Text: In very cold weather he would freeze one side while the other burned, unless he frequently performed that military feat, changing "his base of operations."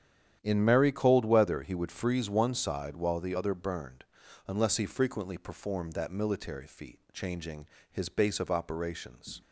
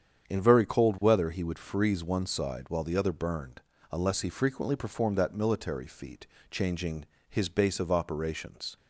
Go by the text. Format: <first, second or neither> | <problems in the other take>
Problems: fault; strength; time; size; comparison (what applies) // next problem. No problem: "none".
second | starts louder than the rest; strong; until 1.4 s; 9.5 dB; strong in the second // says "merry" for "very"; at 0.6 s // pauses between "changing" and "his"; slight; at 7.6 s; 0.26 s long; slight in the second